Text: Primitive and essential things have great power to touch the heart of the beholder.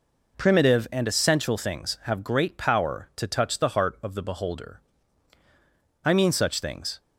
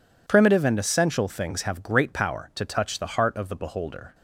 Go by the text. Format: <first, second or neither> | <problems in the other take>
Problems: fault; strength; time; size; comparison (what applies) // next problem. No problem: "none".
second | goes on to say "I mean such things"; noticeable; from 6.0 s on; 0.96 s long